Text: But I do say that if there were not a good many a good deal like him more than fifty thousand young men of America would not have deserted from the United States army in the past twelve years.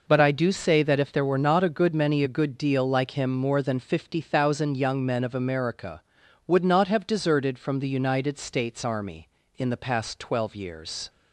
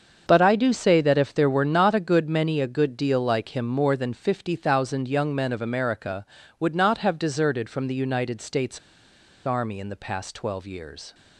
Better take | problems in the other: first | starts louder than the rest; until 1.3 s; 7 dB // pauses between "States" and "army"; noticeable; at 8.7 s; 0.67 s long

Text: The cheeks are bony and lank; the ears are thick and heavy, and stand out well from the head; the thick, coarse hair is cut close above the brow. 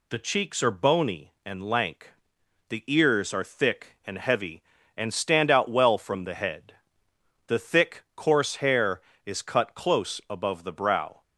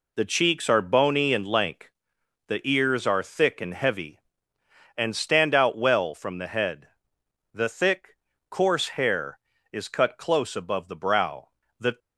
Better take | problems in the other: first | goes on to say "The"; slight; from 11.7 s on; 0.20 s long

